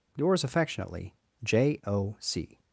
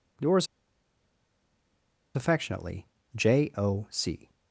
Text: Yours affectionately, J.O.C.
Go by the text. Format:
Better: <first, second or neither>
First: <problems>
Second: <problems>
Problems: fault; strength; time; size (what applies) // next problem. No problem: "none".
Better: first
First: none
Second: pauses between "Yours" and "affectionately"; strong; at 0.4 s; 1.6 s long